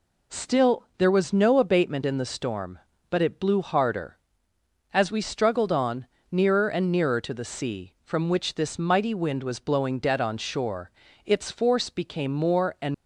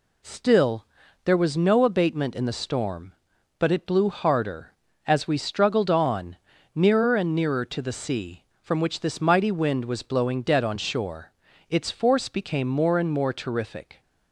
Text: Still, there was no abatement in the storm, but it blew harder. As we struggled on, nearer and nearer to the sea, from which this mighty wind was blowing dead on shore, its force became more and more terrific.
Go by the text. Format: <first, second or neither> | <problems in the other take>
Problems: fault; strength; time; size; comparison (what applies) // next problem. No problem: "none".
second | stops before "more terrific"; at 12.9 s